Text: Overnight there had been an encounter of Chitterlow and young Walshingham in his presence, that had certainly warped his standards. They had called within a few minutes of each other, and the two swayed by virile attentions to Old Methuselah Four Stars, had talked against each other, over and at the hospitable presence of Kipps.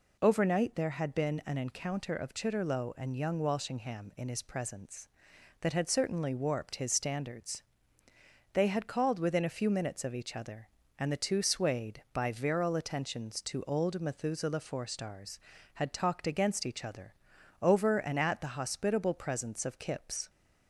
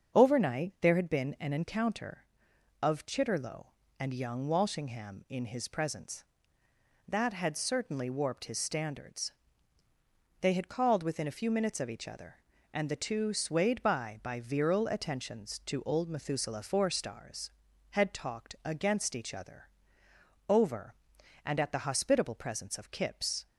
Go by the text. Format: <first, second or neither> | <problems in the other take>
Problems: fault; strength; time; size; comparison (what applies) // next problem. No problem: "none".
first | starts louder than the rest; until 1.2 s; 7 dB // says "by" twice; at 14.2 s